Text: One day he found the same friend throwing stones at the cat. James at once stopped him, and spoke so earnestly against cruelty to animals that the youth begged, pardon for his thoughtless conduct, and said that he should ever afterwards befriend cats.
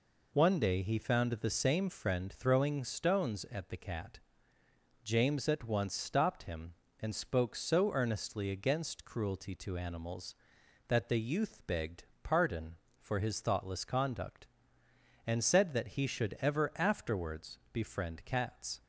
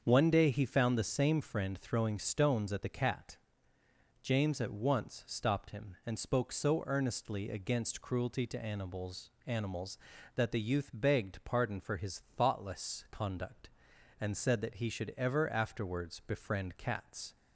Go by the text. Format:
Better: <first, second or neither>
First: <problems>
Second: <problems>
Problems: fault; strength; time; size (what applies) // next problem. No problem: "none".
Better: first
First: none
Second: starts louder than the rest; until 1.0 s; 6.5 dB // says "animals" twice; at 9.4 s